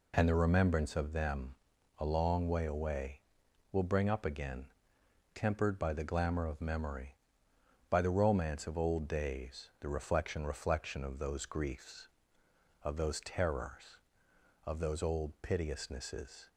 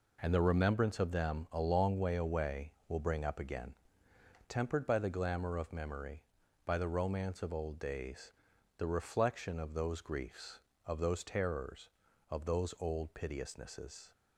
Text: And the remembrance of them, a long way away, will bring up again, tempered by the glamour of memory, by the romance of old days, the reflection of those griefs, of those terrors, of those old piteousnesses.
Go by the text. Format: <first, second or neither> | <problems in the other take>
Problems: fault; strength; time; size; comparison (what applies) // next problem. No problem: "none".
second | says "reflection" twice; at 10.4 s